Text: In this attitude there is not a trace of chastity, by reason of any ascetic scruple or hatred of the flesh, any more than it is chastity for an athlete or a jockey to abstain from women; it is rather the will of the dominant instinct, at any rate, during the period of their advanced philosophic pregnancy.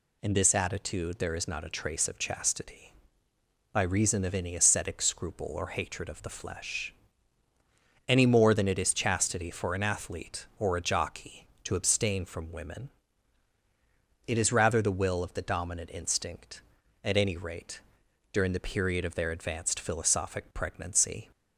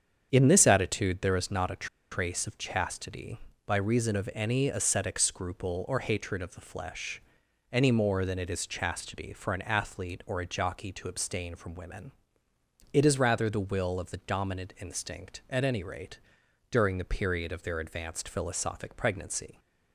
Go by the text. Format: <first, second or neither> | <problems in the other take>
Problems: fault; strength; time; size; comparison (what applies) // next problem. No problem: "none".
first | starts louder than the rest; strong; until 1.3 s; 8 dB // pauses between "a" and "trace"; slight; at 1.8 s; 0.25 s long